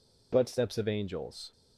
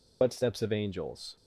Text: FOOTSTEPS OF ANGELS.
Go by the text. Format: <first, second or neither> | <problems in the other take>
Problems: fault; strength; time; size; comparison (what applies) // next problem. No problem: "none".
first | loses the start of "FOOTSTEPS"; at 0.2 s; 40 ms